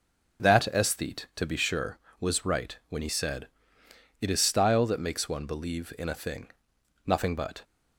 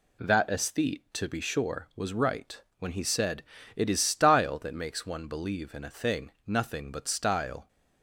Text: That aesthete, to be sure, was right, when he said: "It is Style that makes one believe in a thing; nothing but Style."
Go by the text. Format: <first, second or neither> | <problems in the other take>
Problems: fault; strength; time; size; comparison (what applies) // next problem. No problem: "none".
second | stops before "Style"; at 7.6 s